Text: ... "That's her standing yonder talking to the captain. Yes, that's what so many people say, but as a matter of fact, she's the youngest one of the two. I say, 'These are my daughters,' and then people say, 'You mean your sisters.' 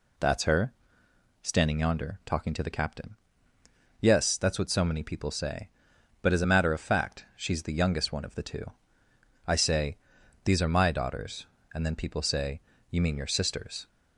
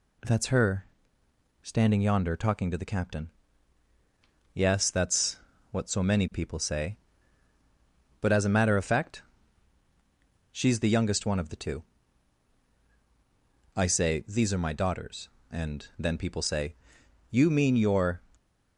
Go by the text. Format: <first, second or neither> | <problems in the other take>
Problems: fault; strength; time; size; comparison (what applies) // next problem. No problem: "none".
first | pauses between "her" and "standing"; noticeable; at 0.8 s; 0.76 s long; noticeable in the first // pauses between "that's" and "what"; slight; at 5.3 s; 0.34 s long // stops before "sisters"; at 18.3 s